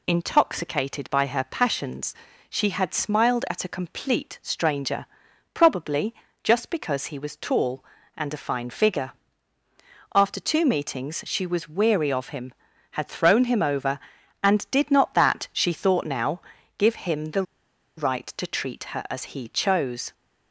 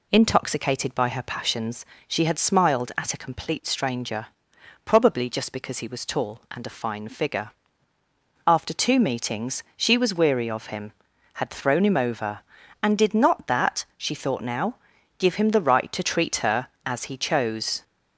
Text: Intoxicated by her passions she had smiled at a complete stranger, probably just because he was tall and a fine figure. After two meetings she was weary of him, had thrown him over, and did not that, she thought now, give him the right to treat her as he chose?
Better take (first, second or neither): second